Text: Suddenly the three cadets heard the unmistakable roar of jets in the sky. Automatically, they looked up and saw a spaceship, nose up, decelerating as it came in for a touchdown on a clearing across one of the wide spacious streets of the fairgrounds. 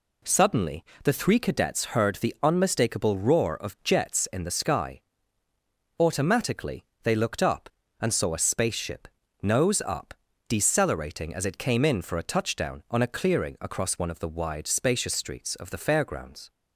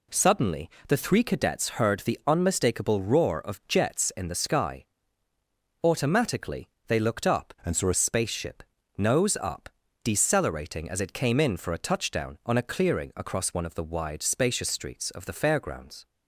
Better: first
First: pauses between "Suddenly" and "the"; slight; at 0.8 s; 0.20 s long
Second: pauses between "Suddenly" and "the"; slight; at 0.6 s; 0.18 s long // changes voice from "and" to "a"; from 7.6 to 7.9 s; 0.3 s long

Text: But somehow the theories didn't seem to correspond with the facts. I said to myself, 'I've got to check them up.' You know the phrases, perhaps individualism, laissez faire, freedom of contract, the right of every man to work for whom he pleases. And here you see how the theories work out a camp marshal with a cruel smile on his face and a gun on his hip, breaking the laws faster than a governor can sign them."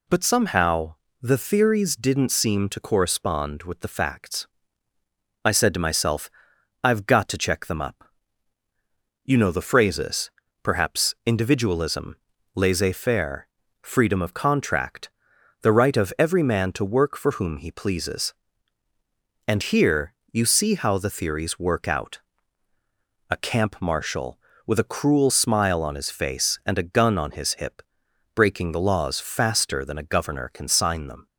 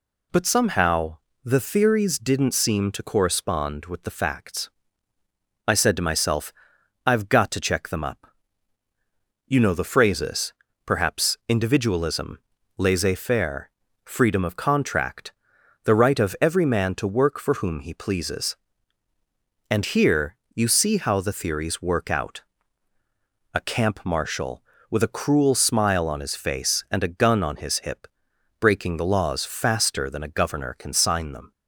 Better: neither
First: pauses between "somehow" and "the"; slight; at 0.9 s; 0.26 s long // pauses between "here" and "you"; slight; at 20.1 s; 0.18 s long // pauses between "out" and "a"; at 22.1 s; 1.1 s long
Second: pauses between "somehow" and "the"; slight; at 1.1 s; 0.26 s long // pauses between "here" and "you"; slight; at 20.3 s; 0.18 s long // pauses between "out" and "a"; at 22.4 s; 1.1 s long

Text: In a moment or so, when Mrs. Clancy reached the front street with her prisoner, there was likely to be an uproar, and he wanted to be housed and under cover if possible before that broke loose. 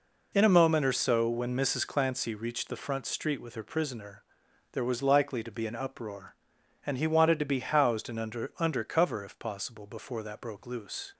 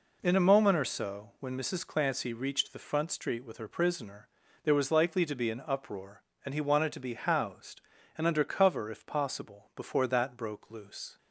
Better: second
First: says "under" twice; at 8.5 s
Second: none

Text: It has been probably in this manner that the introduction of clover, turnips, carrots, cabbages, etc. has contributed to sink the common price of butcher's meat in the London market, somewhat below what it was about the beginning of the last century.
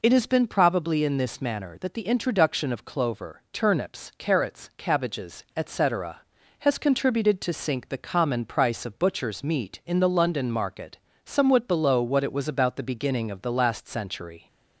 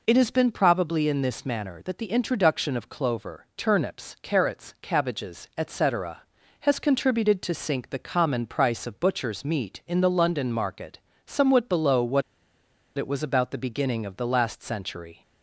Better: first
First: none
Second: pauses between "what" and "it"; noticeable; at 12.2 s; 0.75 s long

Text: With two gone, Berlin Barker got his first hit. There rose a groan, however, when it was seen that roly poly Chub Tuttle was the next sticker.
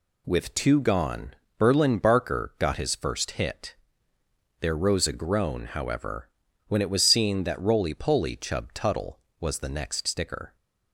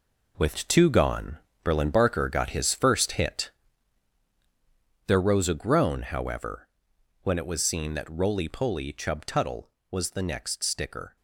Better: first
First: none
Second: gets quieter; strong; throughout; 10 dB

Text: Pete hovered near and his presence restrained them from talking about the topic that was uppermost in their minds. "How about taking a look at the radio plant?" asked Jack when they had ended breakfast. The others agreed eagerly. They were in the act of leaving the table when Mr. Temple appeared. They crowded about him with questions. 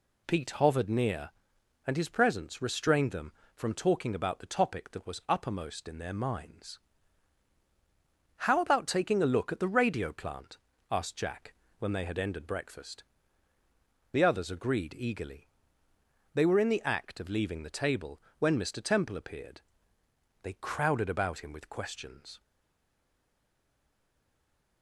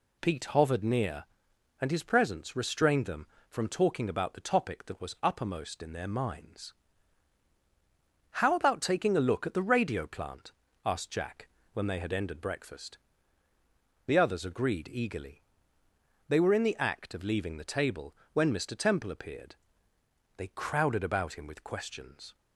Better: second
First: pauses between "Jack" and "when"; slight; at 11.5 s; 0.26 s long // pauses between "table" and "when"; slight; at 18.2 s; 0.18 s long // stays silent after the last word; from 22.4 s on; 2.4 s long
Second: pauses between "Jack" and "when"; slight; at 11.4 s; 0.26 s long // pauses between "table" and "when"; slight; at 18.1 s; 0.18 s long

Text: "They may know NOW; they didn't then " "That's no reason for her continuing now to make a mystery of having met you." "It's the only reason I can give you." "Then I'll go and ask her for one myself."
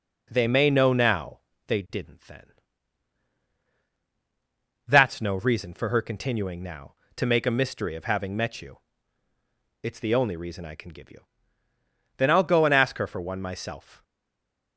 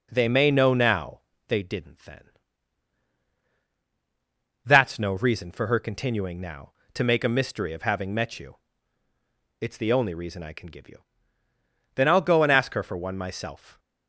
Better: second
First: stays silent after the last word; slight; from 14.0 s on; 0.7 s long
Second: none

